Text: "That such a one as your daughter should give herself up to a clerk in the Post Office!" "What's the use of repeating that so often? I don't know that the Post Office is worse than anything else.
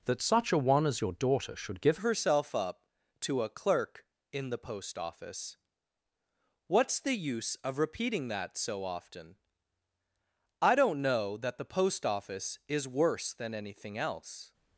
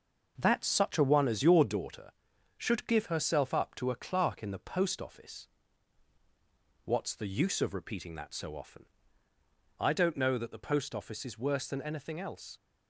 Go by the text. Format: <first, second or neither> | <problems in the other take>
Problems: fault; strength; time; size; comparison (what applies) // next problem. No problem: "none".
second | changes voice at "herself"; from 1.9 s on; 12.6 s long